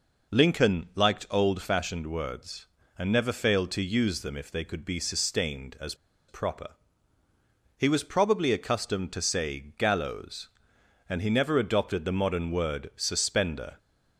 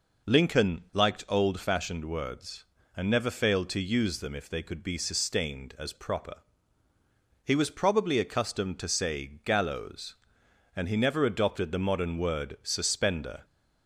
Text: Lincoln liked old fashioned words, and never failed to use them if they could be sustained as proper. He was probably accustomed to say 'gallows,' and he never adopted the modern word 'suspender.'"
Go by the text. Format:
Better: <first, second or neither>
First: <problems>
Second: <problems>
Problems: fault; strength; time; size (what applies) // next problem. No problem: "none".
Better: second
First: pauses between "as" and "proper"; slight; at 5.9 s; 0.34 s long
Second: none